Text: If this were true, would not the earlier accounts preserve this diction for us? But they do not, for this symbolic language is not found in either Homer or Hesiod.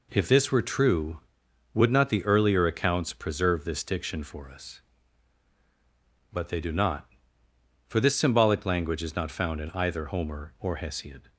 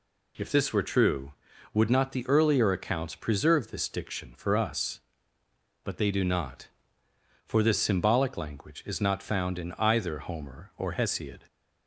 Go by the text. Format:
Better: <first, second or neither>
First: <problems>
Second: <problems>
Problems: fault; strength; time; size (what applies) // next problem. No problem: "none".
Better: neither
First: none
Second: none